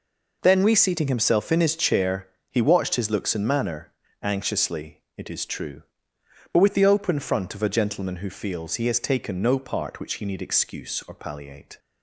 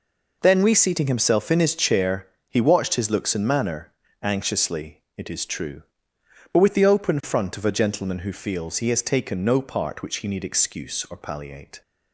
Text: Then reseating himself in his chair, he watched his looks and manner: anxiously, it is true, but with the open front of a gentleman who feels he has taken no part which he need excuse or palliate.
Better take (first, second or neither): neither